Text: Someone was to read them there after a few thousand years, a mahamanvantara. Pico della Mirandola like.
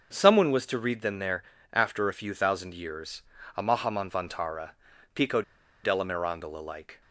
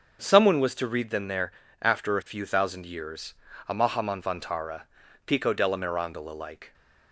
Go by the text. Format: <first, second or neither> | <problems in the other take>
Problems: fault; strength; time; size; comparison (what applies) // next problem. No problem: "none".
second | starts louder than the rest; until 1.1 s; 7 dB; also in the second // pauses between "there" and "after"; slight; at 1.4 s; 0.30 s long; slight in the second // pauses between "Pico" and "della"; at 5.4 s; 0.41 s long